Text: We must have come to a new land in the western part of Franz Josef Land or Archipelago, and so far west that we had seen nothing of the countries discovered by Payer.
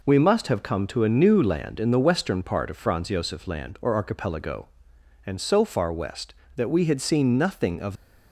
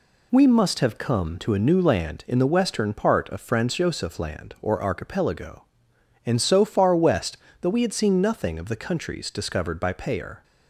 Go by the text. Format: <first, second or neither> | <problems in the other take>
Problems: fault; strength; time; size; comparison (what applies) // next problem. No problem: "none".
second | stops before "the countries discovered by Payer"; at 7.9 s